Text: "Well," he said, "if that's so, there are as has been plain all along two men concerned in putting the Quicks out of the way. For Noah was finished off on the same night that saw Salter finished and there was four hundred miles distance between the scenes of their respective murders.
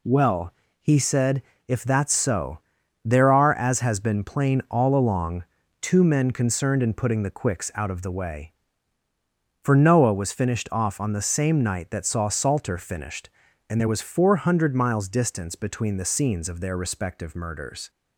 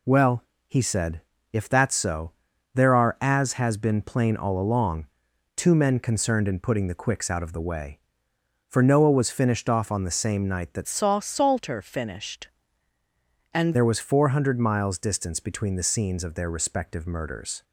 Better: first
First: pauses between "along" and "two"; at 5.4 s; 0.38 s long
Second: pauses between "along" and "two"; noticeable; at 5.0 s; 0.48 s long // changes voice from "saw" to "and"; from 10.8 to 13.7 s; 2.9 s long

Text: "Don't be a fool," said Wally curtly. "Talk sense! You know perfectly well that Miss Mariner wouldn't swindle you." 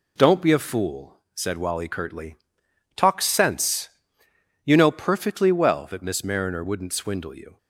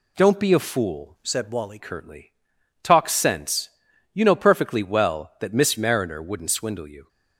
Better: first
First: none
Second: changes voice from "said" to "Wally"; from 1.2 to 1.7 s; 0.5 s long

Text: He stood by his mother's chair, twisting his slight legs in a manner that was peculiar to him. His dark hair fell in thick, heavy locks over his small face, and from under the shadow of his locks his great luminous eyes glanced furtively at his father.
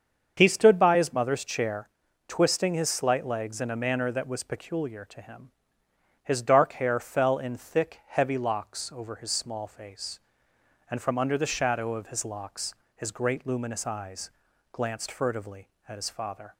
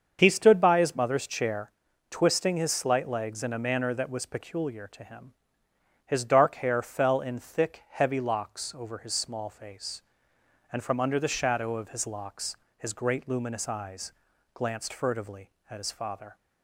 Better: neither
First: starts louder than the rest; until 1.4 s; 7 dB // pauses between "locks" and "his"; slight; at 12.7 s; 0.20 s long // pauses between "eyes" and "glanced"; at 14.2 s; 0.42 s long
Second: starts louder than the rest; until 1.2 s; 7 dB // pauses between "locks" and "his"; slight; at 12.5 s; 0.20 s long // pauses between "eyes" and "glanced"; at 14.1 s; 0.42 s long

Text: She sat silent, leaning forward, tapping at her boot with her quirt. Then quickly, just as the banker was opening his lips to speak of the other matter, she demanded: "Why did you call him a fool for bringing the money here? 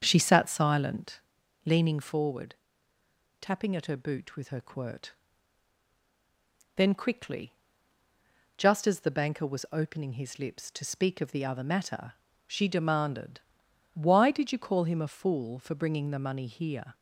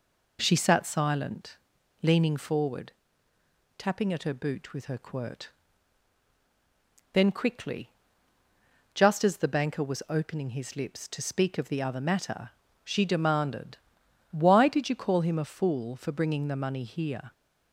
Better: second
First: starts louder than the rest; strong; until 1.3 s; 7.5 dB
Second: none

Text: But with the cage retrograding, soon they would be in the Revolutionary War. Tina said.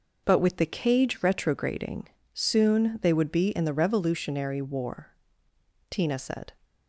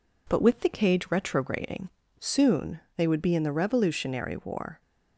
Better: first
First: none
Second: pauses between "soon" and "they"; slight; at 2.7 s; 0.16 s long // stops before "Tina said"; at 4.7 s

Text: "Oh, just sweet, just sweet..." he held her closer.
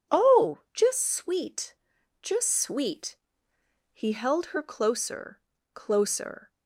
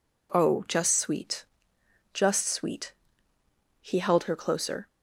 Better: second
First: says "closer" twice; at 5.7 s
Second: none

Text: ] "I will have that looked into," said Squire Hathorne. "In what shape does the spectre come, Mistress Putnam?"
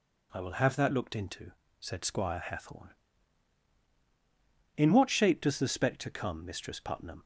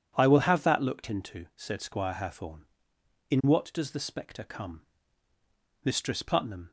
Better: first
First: none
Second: skips "shape"; at 3.7 s

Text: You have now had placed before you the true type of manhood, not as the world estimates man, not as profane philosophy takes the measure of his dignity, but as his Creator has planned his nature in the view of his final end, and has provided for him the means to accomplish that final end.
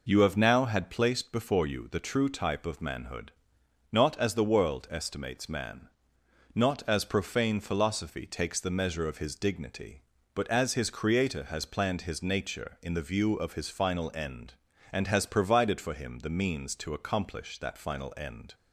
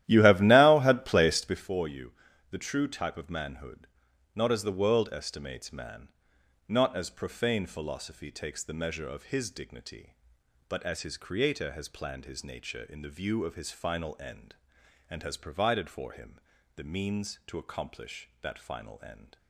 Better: first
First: none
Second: starts louder than the rest; strong; until 1.6 s; 13.5 dB // pauses between "you" and "the"; at 2.1 s; 0.38 s long // pauses between "him" and "the"; slight; at 16.4 s; 0.34 s long

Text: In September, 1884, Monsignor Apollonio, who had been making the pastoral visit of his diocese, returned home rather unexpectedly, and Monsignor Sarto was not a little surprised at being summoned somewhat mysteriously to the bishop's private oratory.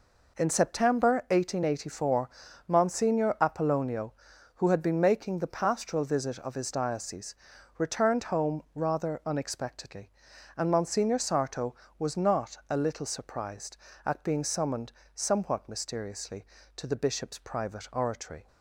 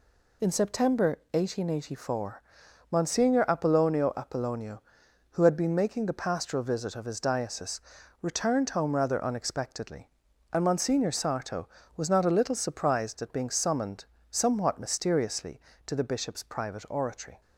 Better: first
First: pauses between "summoned" and "somewhat"; slight; at 14.9 s; 0.22 s long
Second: says "Apollonio" twice; at 4.1 s // pauses between "summoned" and "somewhat"; slight; at 14.0 s; 0.26 s long

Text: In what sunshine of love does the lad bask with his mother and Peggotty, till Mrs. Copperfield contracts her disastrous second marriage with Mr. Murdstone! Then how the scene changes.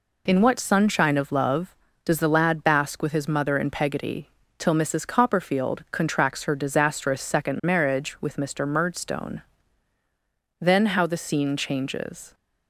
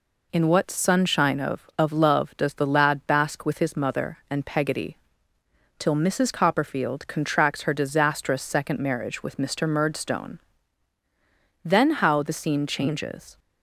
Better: first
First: none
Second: says "of" twice; at 1.7 s

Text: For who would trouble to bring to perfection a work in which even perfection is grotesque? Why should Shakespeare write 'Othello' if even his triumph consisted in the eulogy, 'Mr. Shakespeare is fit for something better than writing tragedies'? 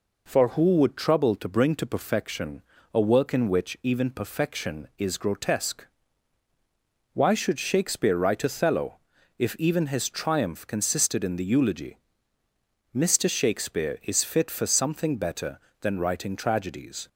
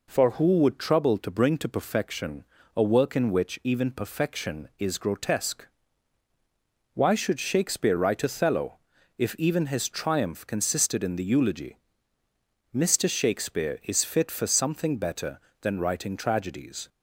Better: neither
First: pauses between "perfection" and "a"; slight; at 2.6 s; 0.32 s long // pauses between "Othello" and "if"; at 8.9 s; 0.40 s long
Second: pauses between "perfection" and "a"; slight; at 2.4 s; 0.32 s long // pauses between "Othello" and "if"; at 8.7 s; 0.40 s long

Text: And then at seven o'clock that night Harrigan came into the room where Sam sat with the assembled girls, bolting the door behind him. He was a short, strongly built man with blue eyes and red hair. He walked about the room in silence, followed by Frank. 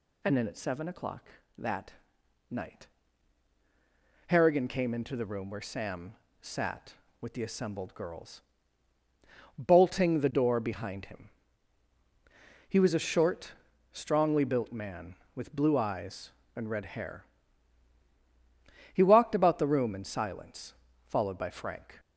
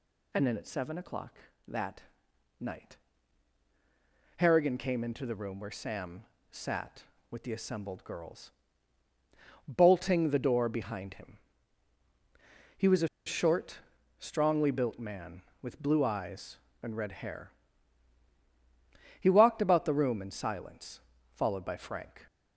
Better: first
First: pauses between "that" and "night"; noticeable; at 1.9 s; 0.58 s long // pauses between "night" and "Harrigan"; strong; at 2.8 s; 1.4 s long // pauses between "Sam" and "sat"; slight; at 6.1 s; 0.26 s long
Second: pauses between "that" and "night"; noticeable; at 2.0 s; 0.58 s long // pauses between "night" and "Harrigan"; strong; at 2.9 s; 1.4 s long // pauses between "Sam" and "sat"; slight; at 6.2 s; 0.26 s long // pauses between "a" and "short"; slight; at 13.0 s; 0.18 s long

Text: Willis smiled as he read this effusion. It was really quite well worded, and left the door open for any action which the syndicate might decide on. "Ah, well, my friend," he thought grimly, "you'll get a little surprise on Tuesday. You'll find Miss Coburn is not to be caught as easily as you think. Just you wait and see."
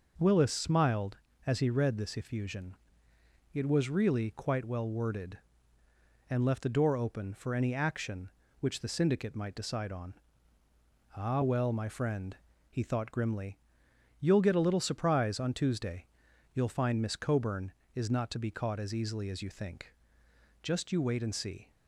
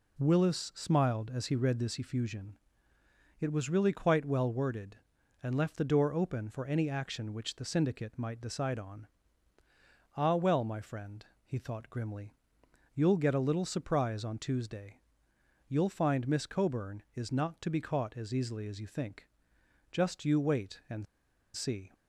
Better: first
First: none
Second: pauses between "and" and "see"; noticeable; at 21.0 s; 0.50 s long

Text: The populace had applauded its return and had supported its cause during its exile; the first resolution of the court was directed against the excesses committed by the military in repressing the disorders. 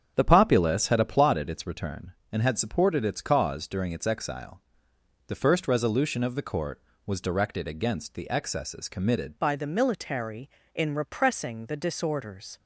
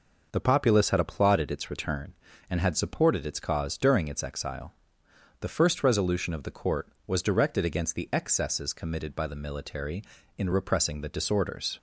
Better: second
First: starts louder than the rest; strong; until 1.1 s; 8.5 dB // changes voice at "by"; from 9.3 s on; 3.2 s long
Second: none

